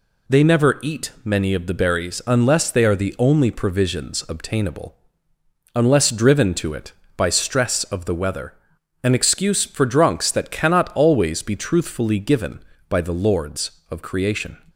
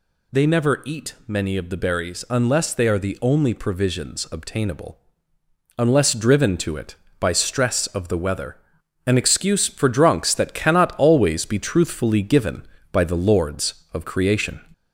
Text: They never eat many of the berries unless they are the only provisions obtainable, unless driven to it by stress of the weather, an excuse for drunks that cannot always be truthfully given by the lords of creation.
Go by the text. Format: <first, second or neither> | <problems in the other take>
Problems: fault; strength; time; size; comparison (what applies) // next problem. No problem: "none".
first | gets louder; slight; throughout; 2.5 dB